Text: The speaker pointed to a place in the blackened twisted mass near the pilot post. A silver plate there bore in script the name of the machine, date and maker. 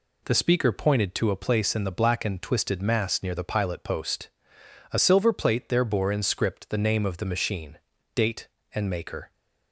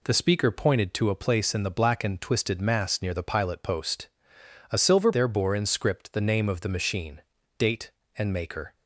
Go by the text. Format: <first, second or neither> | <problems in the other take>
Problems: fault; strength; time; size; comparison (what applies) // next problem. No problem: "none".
first | skips "plate"; at 5.1 s